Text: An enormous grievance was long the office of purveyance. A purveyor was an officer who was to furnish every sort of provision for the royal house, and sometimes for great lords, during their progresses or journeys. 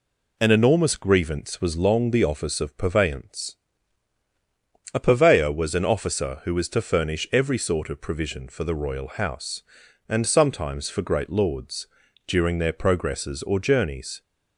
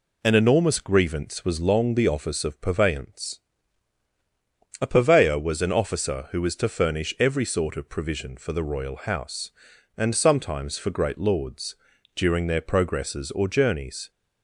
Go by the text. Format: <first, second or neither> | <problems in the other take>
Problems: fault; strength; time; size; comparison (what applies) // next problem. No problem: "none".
neither | none